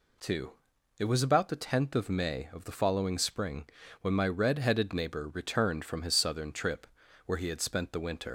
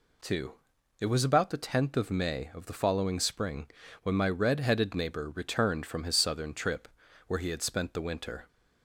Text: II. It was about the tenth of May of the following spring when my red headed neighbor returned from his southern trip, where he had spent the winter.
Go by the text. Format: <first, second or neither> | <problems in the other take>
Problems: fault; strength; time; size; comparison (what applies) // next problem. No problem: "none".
second | pauses between "spring" and "when"; slight; at 3.6 s; 0.34 s long; slight in the second // leaves "winter" unfinished; at 8.2 s; 120 ms